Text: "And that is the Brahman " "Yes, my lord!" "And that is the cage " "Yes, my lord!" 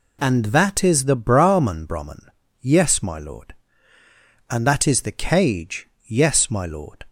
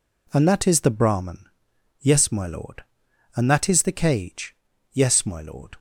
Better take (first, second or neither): second